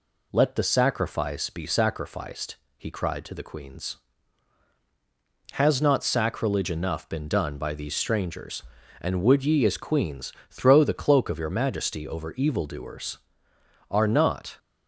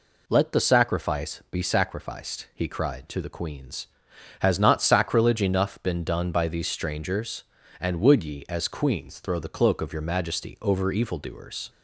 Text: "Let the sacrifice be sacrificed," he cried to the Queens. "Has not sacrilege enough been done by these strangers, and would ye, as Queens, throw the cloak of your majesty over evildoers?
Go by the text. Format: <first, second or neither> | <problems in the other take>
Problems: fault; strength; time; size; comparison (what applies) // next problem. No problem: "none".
second | goes on to say "Are not"; noticeable; from 13.8 s on; 0.70 s long